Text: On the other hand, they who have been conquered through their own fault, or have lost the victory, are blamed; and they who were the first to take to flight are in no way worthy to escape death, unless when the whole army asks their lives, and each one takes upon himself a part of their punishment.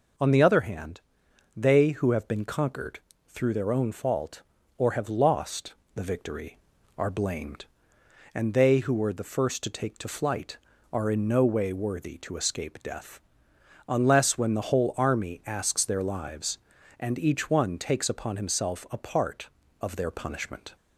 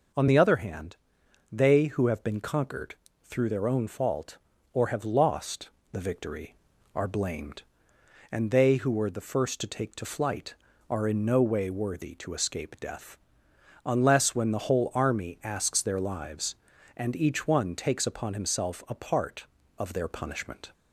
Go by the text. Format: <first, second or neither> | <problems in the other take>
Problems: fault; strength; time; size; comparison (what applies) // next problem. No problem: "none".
neither | pauses between "conquered" and "through"; slight; the same in both // pauses between "lost" and "the"; slight; the same in both